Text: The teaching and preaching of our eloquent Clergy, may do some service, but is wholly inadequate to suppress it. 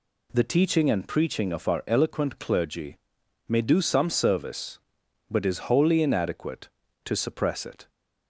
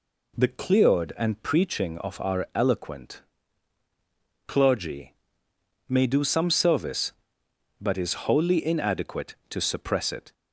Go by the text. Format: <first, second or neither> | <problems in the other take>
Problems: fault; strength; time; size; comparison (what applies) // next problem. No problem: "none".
first | says "cleared" for "teaching"; at 0.4 s // pauses between "eloquent" and "Clergy"; strong; at 3.2 s; 1.2 s long